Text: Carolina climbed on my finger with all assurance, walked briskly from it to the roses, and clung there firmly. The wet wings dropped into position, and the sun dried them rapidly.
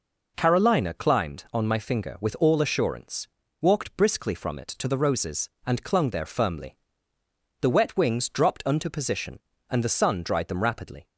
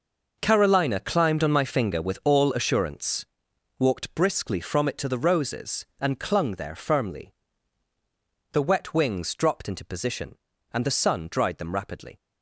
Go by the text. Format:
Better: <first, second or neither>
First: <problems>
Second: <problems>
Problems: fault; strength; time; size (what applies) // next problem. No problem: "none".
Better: second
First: says "unto" for "into"; at 8.6 s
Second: none